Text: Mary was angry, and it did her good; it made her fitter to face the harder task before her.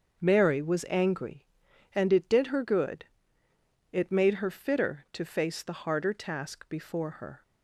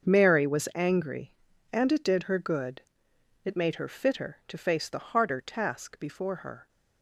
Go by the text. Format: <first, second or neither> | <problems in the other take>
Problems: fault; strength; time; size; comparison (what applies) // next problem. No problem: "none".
neither | starts louder than the rest; the same in both